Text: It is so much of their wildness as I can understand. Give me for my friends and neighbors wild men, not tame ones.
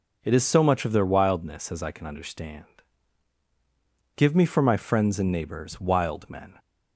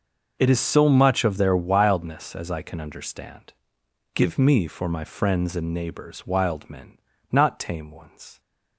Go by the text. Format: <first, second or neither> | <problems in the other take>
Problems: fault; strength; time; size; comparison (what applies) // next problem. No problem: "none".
second | stops before "not tame ones"; at 6.5 s